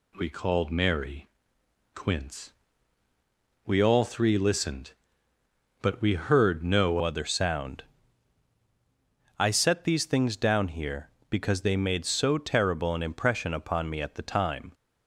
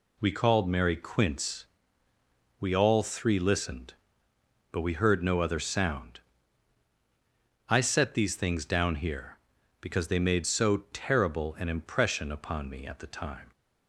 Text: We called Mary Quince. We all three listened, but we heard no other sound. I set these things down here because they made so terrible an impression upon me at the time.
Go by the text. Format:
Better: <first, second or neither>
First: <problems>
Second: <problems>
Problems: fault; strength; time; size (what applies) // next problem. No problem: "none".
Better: second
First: pauses between "Mary" and "Quince"; noticeable; at 1.2 s; 0.68 s long // changes voice at "other"; from 7.0 s on; 7.7 s long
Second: none